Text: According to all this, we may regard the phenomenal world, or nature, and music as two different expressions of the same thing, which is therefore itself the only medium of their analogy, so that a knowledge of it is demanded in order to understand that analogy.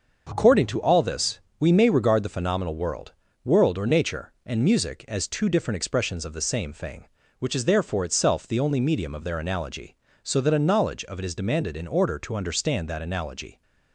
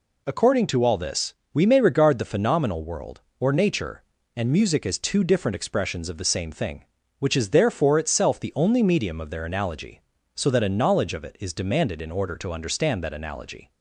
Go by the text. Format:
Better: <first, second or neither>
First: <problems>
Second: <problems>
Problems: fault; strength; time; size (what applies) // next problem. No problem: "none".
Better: second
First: starts louder than the rest; until 1.3 s; 6.5 dB // says "world" twice; at 3.4 s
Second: none